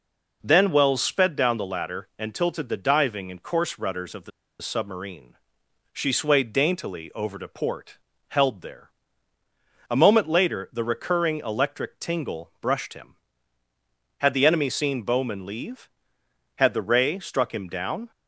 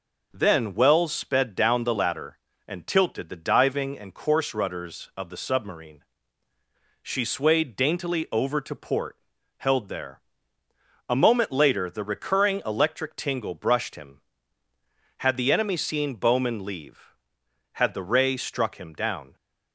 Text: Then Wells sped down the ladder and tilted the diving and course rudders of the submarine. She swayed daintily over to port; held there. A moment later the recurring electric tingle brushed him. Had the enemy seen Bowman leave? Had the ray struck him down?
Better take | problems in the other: second | pauses between "the" and "submarine"; slight; at 4.3 s; 0.30 s long

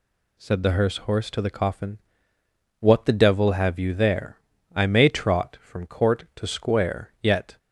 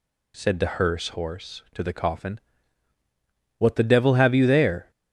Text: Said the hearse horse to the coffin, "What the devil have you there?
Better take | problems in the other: second | goes on to say "I may trot from court to square Yet"; strong; from 4.7 s on; 2.8 s long

